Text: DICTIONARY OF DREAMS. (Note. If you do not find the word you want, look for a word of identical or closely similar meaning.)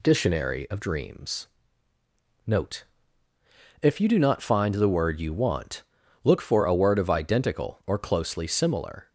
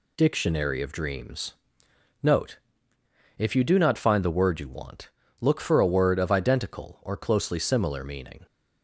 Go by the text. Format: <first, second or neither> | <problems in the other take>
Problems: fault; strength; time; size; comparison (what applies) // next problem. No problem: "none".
second | stops before "meaning"; at 9.0 s